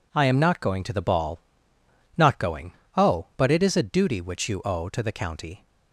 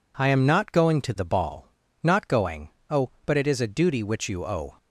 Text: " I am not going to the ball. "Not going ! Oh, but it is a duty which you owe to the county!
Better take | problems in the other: first | stops before "to the county"; at 4.7 s

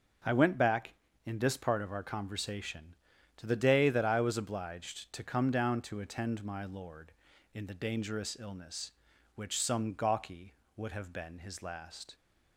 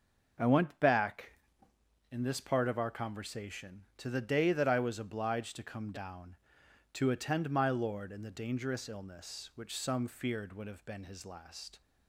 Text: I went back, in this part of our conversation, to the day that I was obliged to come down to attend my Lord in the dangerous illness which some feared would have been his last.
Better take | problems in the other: second | starts louder than the rest; until 1.5 s; 6.5 dB // says "gawky" for "feared"; at 9.9 s

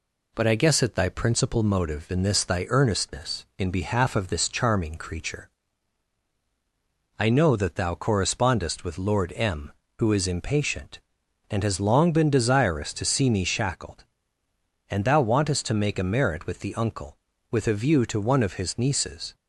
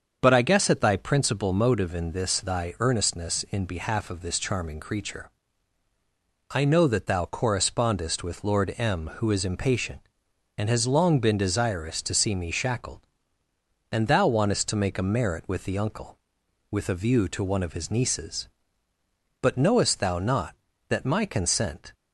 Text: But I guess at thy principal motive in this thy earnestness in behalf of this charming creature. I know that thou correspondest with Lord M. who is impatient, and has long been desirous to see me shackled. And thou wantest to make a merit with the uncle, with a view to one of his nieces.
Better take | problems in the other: first | starts louder than the rest; until 1.2 s; 7 dB // goes on to say "But knowest thou not that my consent"; strong; from 19.3 s on; 2.5 s long

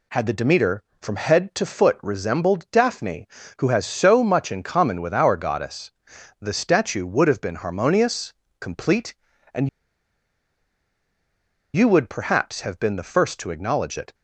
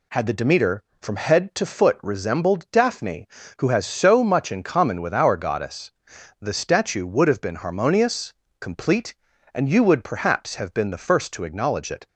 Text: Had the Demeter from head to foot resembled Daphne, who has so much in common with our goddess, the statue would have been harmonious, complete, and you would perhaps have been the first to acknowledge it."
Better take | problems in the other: second | pauses between "and" and "you"; strong; at 9.6 s; 2.0 s long

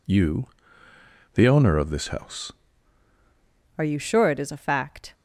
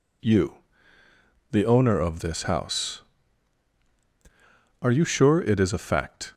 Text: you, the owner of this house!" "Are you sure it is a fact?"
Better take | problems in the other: second | changes voice at "Are"; from 3.7 s on; 1.4 s long

